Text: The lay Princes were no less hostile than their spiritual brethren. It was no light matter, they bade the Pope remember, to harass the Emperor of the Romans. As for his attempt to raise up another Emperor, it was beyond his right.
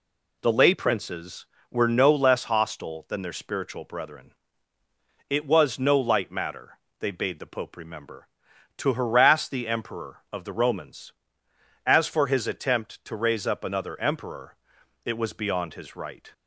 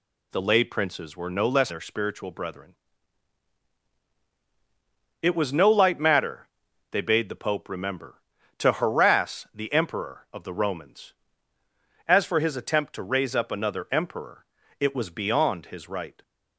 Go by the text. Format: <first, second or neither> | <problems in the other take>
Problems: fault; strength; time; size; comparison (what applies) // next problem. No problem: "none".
first | skips "hostile than"; at 1.6 s